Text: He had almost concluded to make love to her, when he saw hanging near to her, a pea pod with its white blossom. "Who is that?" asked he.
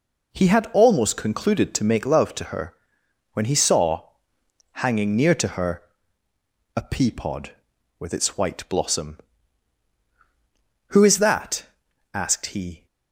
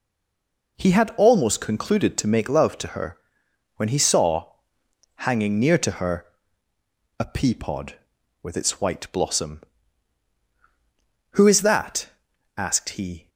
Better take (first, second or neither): first